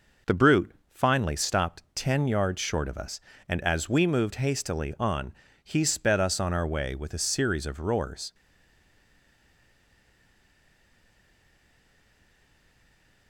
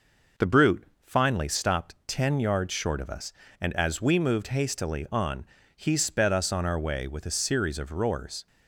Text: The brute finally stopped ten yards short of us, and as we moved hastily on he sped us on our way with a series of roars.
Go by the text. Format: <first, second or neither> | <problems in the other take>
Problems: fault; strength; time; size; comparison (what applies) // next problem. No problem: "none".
second | pauses between "brute" and "finally"; slight; at 0.7 s; 0.22 s long; slight in the second // pauses between "on" and "he"; slight; at 5.3 s; 0.28 s long; slight in the second // stays silent after the last word; strong; from 8.3 s on; 4.9 s long